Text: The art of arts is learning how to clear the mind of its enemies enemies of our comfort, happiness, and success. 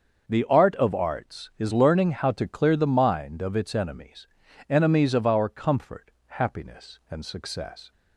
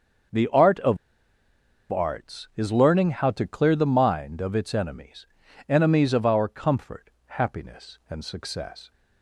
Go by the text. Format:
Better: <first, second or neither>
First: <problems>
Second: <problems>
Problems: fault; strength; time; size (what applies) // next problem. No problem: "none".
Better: first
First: starts louder than the rest; until 1.3 s; 6.5 dB // pauses between "enemies" and "enemies"; at 4.2 s; 0.42 s long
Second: starts louder than the rest; until 2.3 s; 6.5 dB // pauses between "of" and "arts"; noticeable; at 0.9 s; 0.95 s long // pauses between "enemies" and "enemies"; at 5.2 s; 0.42 s long